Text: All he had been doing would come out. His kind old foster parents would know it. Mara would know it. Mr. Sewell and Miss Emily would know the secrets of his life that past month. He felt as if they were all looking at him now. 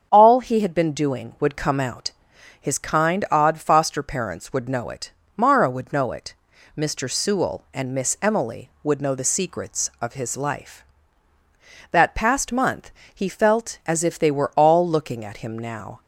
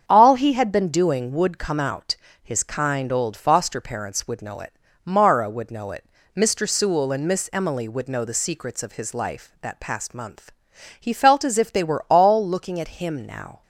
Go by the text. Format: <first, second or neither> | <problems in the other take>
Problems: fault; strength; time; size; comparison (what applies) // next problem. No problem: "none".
second | starts louder than the rest; strong; until 1.1 s; 7.5 dB; strong in the second // says "odd" for "old"; at 3.2 s